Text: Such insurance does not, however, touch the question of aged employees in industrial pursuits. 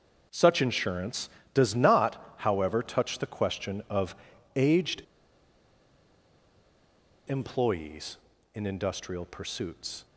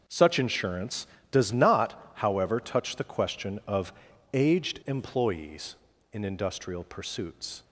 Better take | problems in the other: second | starts louder than the rest; until 1.5 s; 6.5 dB; also in the second // pauses between "of" and "aged"; at 4.1 s; 0.40 s long; also in the second // pauses between "aged" and "employees"; strong; at 5.0 s; 2.2 s long

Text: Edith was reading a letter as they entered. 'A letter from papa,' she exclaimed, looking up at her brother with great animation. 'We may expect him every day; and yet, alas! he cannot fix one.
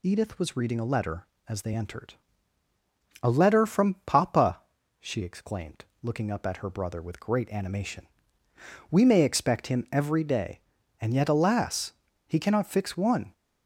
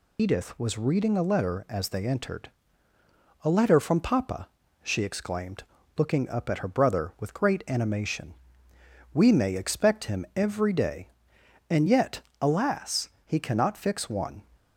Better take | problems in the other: first | loses the start of "Edith"; at 0.1 s; 85 ms

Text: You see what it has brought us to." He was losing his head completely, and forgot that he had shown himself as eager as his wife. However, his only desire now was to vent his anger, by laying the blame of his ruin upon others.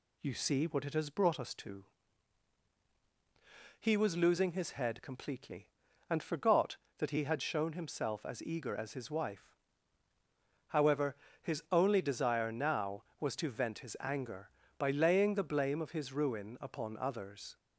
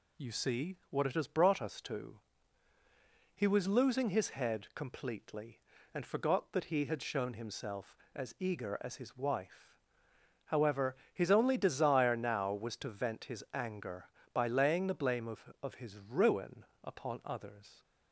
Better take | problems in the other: first | says "of" twice; at 15.6 s // pauses between "ruin" and "upon"; slight; at 16.6 s; 0.20 s long

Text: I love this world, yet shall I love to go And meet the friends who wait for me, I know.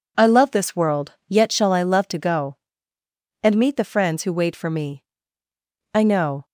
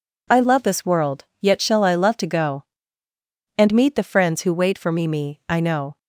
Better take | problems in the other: first | says "me" twice; at 5.0 s

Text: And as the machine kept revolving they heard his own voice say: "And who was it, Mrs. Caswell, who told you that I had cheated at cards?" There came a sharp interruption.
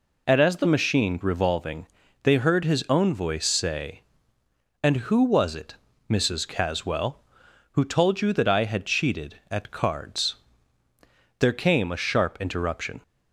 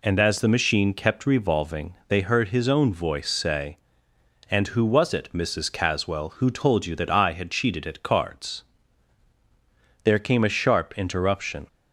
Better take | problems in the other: second | skips "kept"; at 1.2 s // pauses between "revolving" and "they"; at 1.8 s; 0.38 s long

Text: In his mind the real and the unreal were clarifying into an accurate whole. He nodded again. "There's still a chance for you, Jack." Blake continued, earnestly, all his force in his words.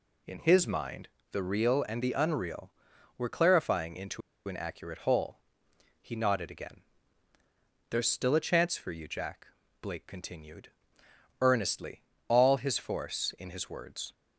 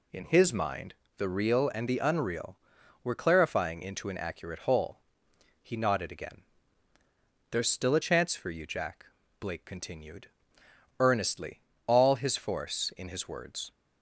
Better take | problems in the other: second | pauses between "mind" and "the"; slight; at 1.0 s; 0.24 s long; slight in the second // pauses between "into" and "an"; slight; at 4.2 s; 0.26 s long

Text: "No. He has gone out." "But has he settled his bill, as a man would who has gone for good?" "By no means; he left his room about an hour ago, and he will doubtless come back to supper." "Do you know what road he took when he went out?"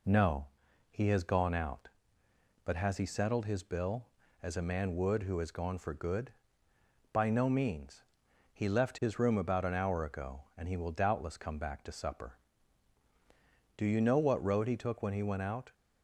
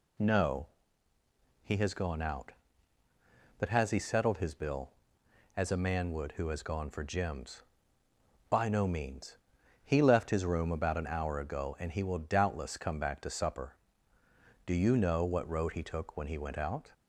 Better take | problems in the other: first | says "gems" for "good"; at 7.0 s

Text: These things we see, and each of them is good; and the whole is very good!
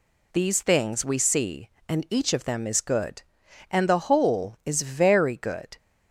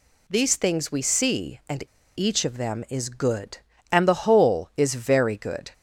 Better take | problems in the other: first | pauses between "and" and "each"; slight; at 1.8 s; 0.30 s long

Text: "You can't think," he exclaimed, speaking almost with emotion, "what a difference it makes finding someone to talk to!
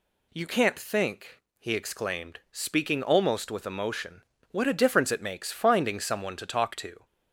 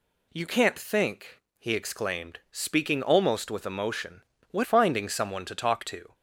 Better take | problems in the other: first | skips "a difference it makes"; at 4.6 s

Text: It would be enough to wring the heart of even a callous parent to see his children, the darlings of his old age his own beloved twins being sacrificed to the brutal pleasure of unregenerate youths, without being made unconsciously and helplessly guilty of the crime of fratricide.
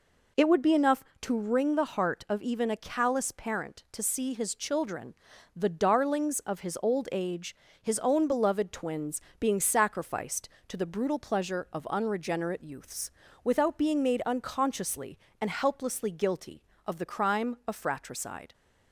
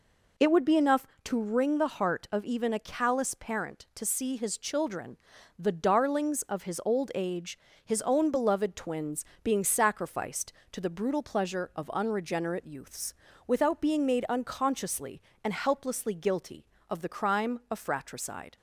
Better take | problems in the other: neither | pauses between "age" and "his"; slight; the same in both // pauses between "twins" and "being"; slight; the same in both

